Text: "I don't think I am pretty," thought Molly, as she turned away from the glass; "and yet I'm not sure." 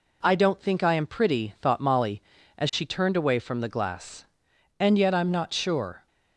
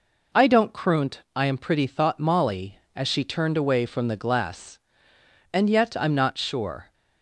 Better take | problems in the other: first | says "croont" for "think"; at 0.7 s

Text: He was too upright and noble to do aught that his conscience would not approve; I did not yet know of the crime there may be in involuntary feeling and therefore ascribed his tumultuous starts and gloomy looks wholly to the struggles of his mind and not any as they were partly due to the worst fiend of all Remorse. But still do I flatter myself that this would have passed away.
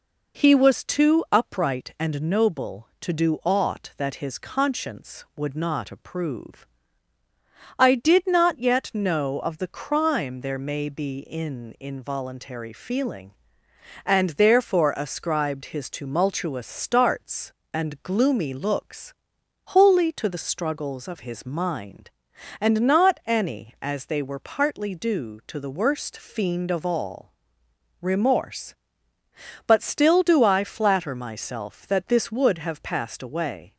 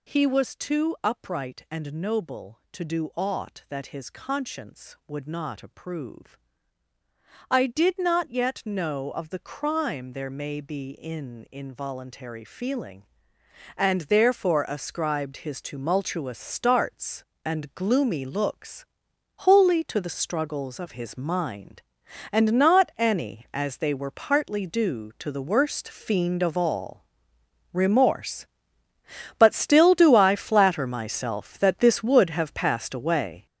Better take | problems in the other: first | gets louder; strong; throughout; 9 dB // pauses between "looks" and "wholly"; noticeable; at 18.8 s; 0.54 s long; noticeable in the first // pauses between "all" and "Remorse"; noticeable; at 27.0 s; 0.70 s long; noticeable in the first

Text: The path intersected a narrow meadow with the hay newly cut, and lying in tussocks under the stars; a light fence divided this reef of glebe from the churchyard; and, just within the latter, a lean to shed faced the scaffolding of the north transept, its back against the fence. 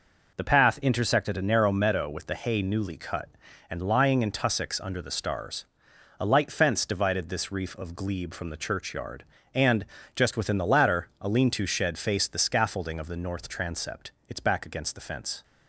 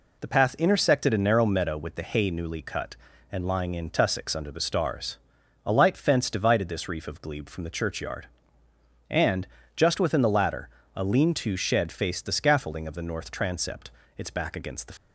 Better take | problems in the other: first | stops before "fence"; at 14.9 s

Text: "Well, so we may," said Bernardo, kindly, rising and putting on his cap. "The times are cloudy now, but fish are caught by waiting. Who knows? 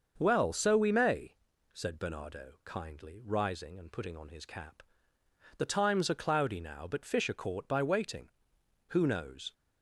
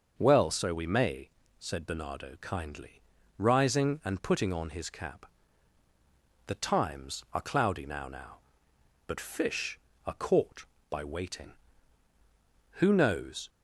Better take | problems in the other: first | starts louder than the rest; until 1.2 s; 6.5 dB; also in the first // says "now" twice; at 8.0 s

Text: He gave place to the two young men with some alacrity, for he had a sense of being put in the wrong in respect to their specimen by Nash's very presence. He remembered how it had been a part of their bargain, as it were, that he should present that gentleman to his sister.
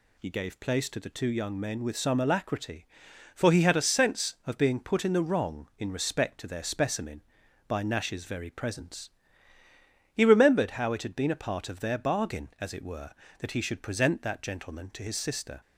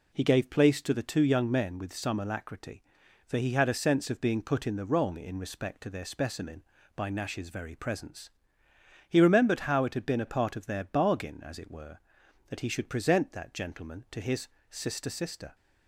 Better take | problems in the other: first | pauses between "his" and "sister"; slight; at 14.4 s; 0.22 s long // says "sister" twice; at 15.0 s

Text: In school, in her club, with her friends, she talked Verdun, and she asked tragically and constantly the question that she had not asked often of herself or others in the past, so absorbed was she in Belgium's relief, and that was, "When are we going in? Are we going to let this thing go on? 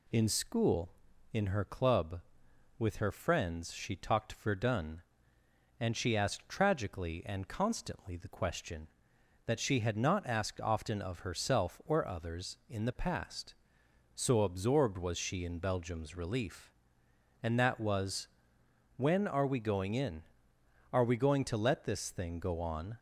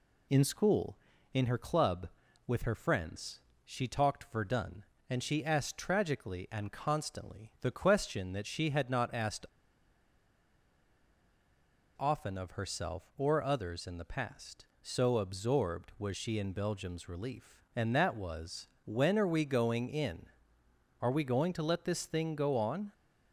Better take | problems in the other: first | pauses between "asked" and "often"; strong; at 9.4 s; 2.5 s long

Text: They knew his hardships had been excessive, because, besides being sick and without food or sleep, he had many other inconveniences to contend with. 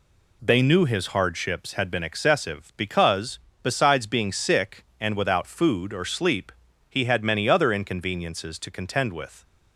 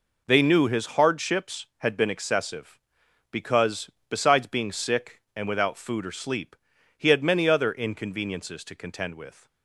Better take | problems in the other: neither | none

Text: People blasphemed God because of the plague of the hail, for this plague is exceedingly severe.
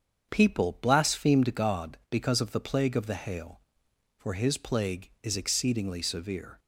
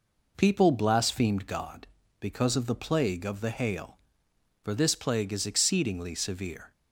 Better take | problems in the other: second | starts louder than the rest; strong; until 1.3 s; 7.5 dB // says "his" for "this"; at 4.3 s

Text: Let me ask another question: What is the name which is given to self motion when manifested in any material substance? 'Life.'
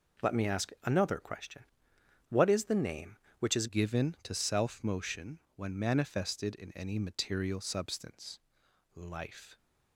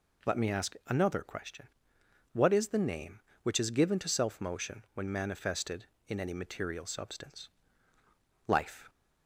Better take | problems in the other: second | changes voice at "given"; from 3.6 s on; 5.9 s long // pauses between "motion" and "when"; slight; at 5.3 s; 0.16 s long

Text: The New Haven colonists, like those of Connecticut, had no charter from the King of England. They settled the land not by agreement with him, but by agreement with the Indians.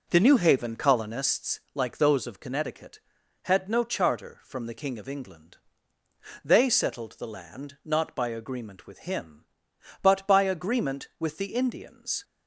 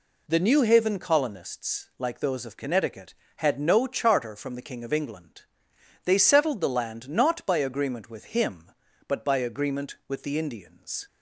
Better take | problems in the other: second | starts louder than the rest; noticeable; until 1.4 s; 4.5 dB

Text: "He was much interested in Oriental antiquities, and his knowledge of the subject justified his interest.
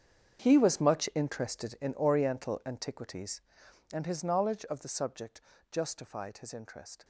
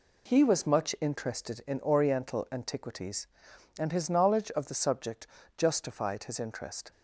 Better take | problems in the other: second | gets quieter; strong; throughout; 16 dB // pauses between "subject" and "justified"; slight; at 5.3 s; 0.32 s long; slight in the second

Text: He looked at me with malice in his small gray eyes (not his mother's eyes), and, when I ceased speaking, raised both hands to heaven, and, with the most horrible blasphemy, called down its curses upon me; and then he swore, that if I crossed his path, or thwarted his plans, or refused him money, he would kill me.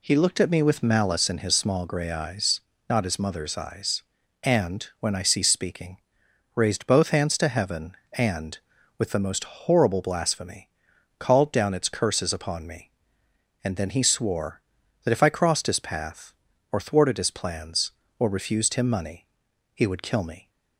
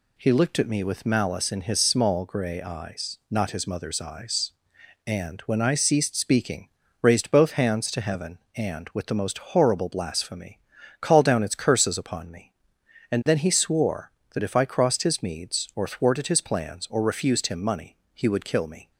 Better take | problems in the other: first | pauses between "most" and "horrible"; slight; at 9.3 s; 0.16 s long // says "meads" for "path"; at 15.2 s

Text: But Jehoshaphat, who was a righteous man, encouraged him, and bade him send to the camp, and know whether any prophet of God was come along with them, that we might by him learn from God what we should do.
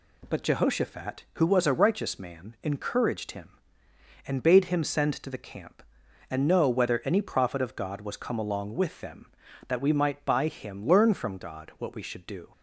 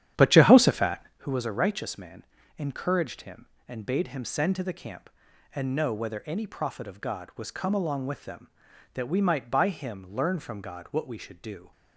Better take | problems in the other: first | starts louder than the rest; strong; until 1.2 s; 10.5 dB

